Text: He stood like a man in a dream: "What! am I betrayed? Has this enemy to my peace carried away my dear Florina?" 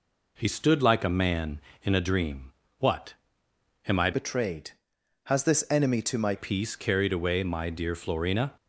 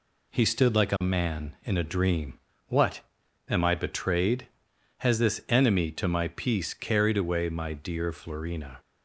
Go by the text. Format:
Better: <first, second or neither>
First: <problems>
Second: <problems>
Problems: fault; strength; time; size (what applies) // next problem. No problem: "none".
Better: second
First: changes voice from "betrayed" to "my"; from 4.1 to 6.3 s; 2.2 s long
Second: none